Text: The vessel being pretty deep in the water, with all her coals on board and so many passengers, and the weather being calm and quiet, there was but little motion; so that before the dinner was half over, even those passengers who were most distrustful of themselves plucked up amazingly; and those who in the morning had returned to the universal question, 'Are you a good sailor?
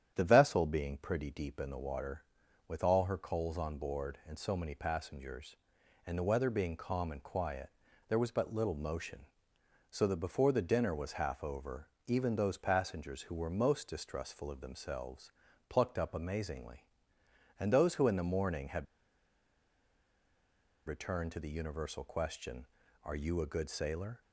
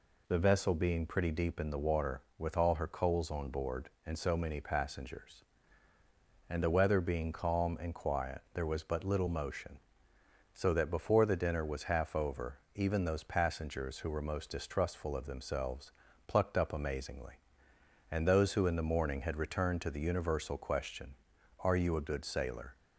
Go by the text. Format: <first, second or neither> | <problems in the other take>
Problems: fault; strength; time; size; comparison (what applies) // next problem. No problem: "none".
second | starts louder than the rest; strong; until 1.1 s; 9.5 dB // pauses between "themselves" and "plucked"; slight; at 15.3 s; 0.36 s long; slight in the second // pauses between "had" and "returned"; strong; at 18.8 s; 2.0 s long